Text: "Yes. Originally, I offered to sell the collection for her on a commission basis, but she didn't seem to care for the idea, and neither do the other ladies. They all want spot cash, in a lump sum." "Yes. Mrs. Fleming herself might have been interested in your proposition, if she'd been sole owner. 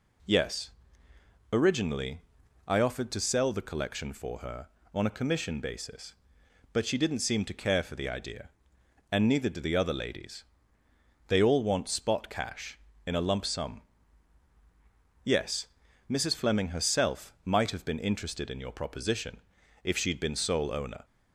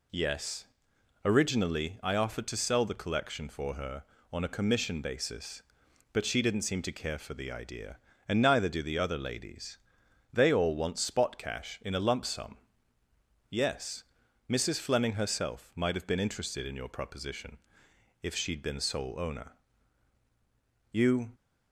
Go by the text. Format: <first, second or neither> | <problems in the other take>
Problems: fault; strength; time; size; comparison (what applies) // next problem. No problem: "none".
first | goes on to say "You"; slight; from 20.9 s on; 0.40 s long